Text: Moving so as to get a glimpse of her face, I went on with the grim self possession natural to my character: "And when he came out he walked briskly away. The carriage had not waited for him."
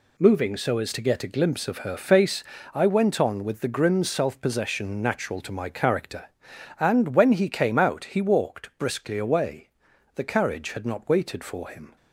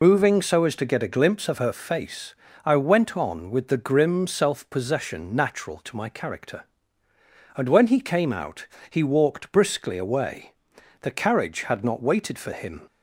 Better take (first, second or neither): first